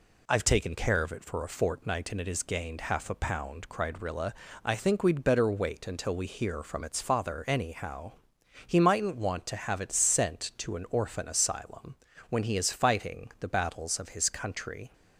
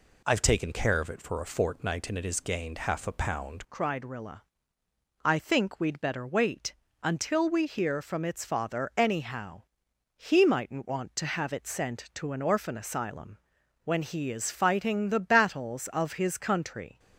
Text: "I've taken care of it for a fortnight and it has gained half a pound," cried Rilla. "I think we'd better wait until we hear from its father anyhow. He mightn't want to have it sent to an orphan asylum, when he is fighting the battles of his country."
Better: first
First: none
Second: changes voice at "cried"; from 3.7 s on; 13.2 s long // pauses between "wait" and "until"; slight; at 6.7 s; 0.28 s long

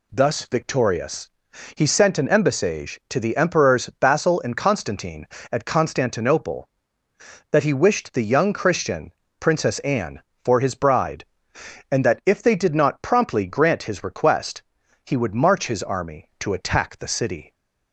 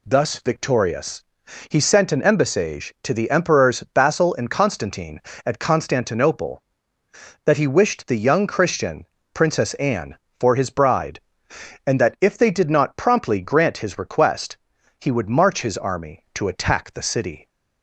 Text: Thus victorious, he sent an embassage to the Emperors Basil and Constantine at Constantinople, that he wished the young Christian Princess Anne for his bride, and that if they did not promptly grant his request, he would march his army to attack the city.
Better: neither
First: pauses between "Christian" and "Princess"; slight; at 9.1 s; 0.28 s long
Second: pauses between "Christian" and "Princess"; slight; at 9.0 s; 0.28 s long

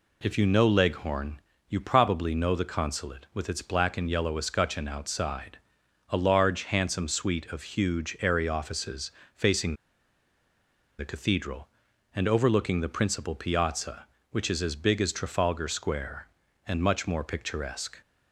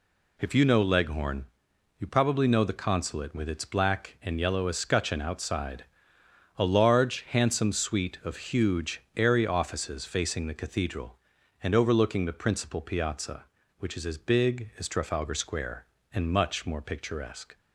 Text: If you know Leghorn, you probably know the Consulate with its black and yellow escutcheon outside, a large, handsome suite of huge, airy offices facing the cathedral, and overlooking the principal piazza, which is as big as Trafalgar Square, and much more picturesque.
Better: second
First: pauses between "offices" and "facing"; slight; at 9.0 s; 0.24 s long // pauses between "facing" and "the"; strong; at 9.7 s; 1.2 s long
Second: none

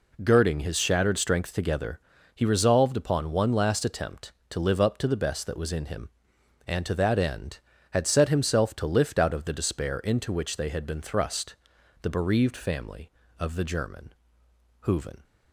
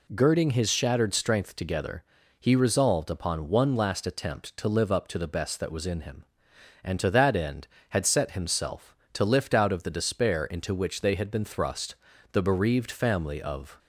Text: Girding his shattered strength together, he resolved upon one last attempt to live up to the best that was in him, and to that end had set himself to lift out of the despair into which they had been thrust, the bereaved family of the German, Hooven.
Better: first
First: none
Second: stops before "the German Hooven"; at 13.7 s

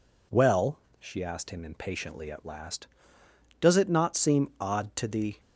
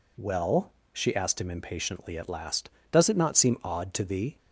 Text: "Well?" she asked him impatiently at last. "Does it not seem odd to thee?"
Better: neither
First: none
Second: none

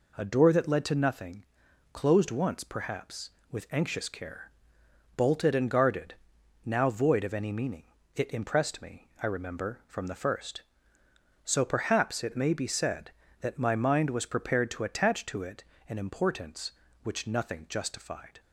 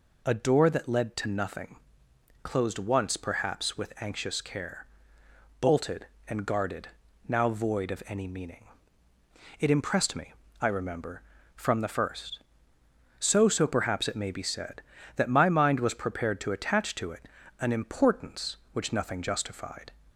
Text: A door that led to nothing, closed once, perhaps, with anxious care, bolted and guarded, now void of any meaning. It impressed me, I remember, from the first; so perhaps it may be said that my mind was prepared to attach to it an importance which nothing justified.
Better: first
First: pauses between "it" and "an"; slight; at 15.6 s; 0.24 s long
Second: says "so" twice; at 13.4 s // pauses between "it" and "an"; slight; at 17.2 s; 0.32 s long

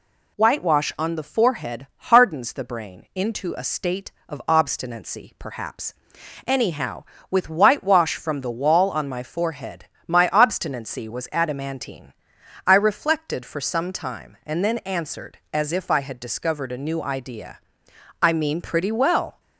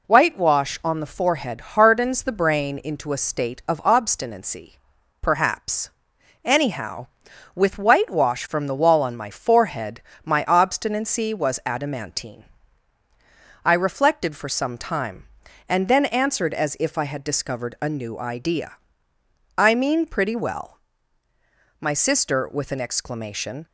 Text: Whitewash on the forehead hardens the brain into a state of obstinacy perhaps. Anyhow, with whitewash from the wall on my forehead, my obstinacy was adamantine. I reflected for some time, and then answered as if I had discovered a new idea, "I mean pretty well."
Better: first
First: none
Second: pauses between "obstinacy" and "perhaps"; at 4.7 s; 0.44 s long // goes on to say "My sister with an exclamation"; strong; from 21.8 s on; 1.8 s long

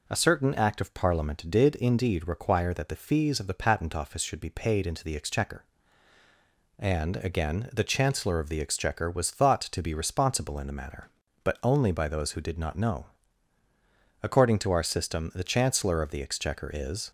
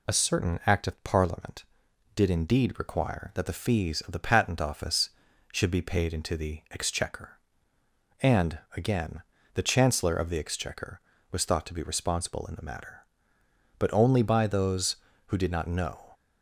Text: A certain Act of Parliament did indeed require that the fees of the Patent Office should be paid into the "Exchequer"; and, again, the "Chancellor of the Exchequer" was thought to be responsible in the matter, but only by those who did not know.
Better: second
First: goes on to say "According to our system the Chancellor of the Exchequer is"; strong; from 14.2 s on; 2.8 s long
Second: none

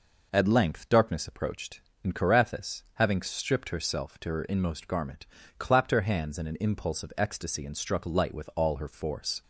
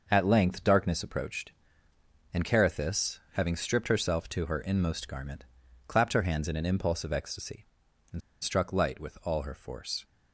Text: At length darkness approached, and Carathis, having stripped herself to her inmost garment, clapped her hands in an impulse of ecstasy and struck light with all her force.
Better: first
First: none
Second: pauses between "and" and "struck"; slight; at 8.2 s; 0.23 s long

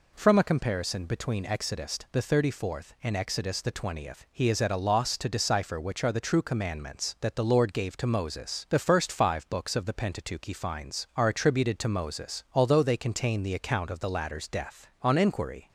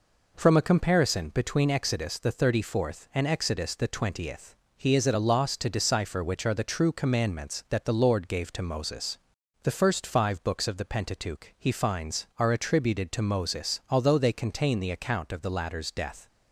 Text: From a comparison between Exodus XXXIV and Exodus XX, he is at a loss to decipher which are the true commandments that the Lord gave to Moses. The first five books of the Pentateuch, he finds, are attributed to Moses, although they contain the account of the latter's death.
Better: second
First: goes on to say "On inquiry"; noticeable; from 15.0 s on; 0.66 s long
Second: none

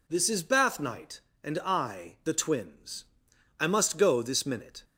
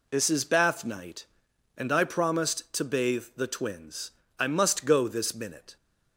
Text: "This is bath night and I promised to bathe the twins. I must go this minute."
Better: second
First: skips "promised to bathe"; at 2.2 s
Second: none

